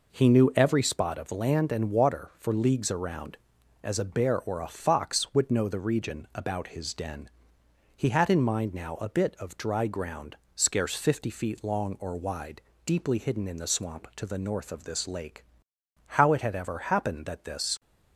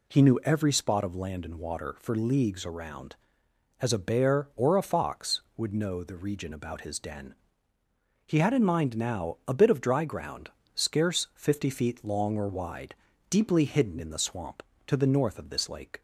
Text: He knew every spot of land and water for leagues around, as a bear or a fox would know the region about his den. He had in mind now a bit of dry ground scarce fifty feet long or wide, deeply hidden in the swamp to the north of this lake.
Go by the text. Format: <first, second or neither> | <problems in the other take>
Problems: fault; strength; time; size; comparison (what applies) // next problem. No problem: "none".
second | pauses between "ground" and "scarce"; slight; at 10.3 s; 0.20 s long; slight in the second // goes on to say "How it had ever happened that this"; strong; from 16.0 s on; 1.7 s long